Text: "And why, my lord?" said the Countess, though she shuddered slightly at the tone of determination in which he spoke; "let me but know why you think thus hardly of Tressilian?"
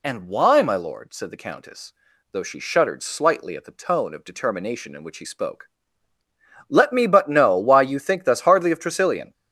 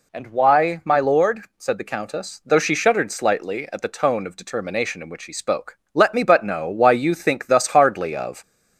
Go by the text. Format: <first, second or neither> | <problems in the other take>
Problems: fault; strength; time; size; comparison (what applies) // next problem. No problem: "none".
first | stops before "Tressilian"; at 8.4 s